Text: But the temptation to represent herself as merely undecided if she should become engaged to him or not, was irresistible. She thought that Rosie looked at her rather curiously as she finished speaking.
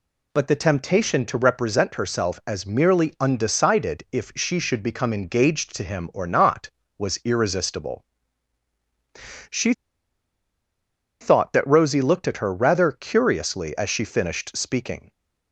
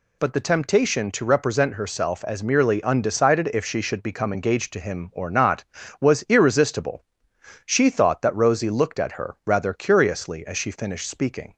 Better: second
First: pauses between "She" and "thought"; strong; at 9.7 s; 1.4 s long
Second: none

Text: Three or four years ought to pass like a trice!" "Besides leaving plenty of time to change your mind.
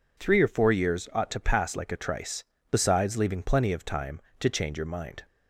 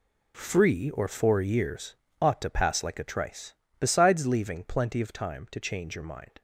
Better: first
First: none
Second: says "Free" for "Three"; at 0.3 s // pauses between "years" and "ought"; slight; at 1.9 s; 0.24 s long

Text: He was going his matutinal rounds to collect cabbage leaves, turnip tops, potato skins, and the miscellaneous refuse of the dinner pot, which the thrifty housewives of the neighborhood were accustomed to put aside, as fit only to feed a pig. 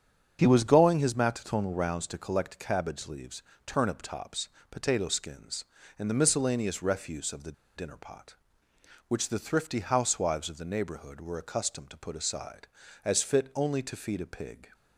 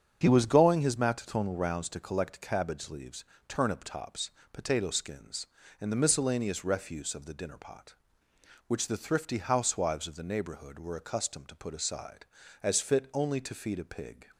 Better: second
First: starts louder than the rest; strong; until 1.4 s; 7.5 dB // pauses between "the" and "dinner"; slight; at 7.5 s; 0.24 s long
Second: starts louder than the rest; strong; until 1.2 s; 7.5 dB

